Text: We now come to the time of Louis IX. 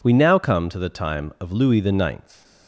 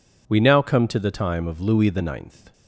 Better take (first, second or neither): neither